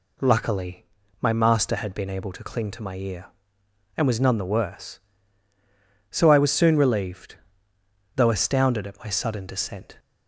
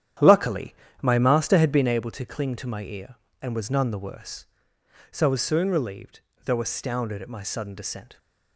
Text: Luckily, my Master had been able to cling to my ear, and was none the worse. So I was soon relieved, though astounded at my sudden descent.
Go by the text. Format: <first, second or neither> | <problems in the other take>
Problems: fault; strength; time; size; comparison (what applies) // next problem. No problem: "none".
first | starts louder than the rest; strong; until 2.0 s; 10 dB